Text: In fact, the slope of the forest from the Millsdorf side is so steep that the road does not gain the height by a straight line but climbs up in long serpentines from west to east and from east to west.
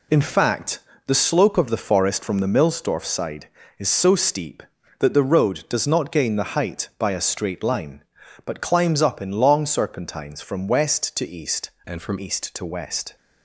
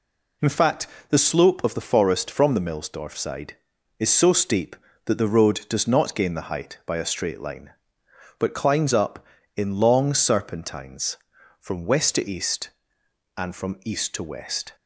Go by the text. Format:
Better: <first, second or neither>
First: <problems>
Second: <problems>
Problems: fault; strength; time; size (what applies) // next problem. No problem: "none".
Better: second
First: changes voice from "and" to "from"; from 11.8 to 12.1 s; 0.3 s long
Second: none